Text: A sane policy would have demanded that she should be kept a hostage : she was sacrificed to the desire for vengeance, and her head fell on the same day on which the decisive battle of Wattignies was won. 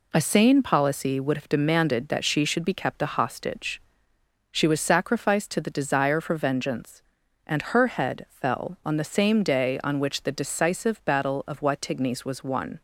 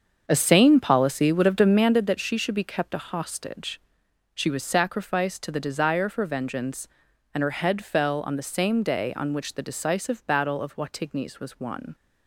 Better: first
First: none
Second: starts louder than the rest; until 2.1 s; 7 dB

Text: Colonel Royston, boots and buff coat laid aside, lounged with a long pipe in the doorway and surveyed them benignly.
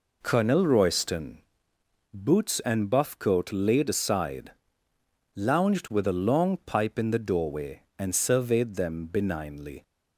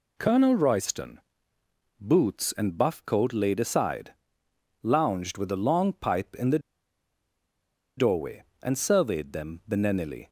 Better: first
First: none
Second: pauses between "the" and "doorway"; strong; at 6.5 s; 1.3 s long

